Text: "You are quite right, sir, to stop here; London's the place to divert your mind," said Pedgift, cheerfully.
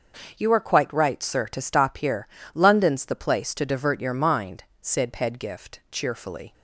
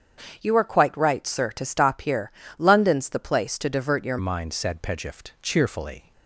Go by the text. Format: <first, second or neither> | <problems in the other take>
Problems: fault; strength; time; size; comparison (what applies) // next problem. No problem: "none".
first | starts louder than the rest; strong; until 1.4 s; 7.5 dB // changes voice at "mind"; from 4.1 s on; 2.0 s long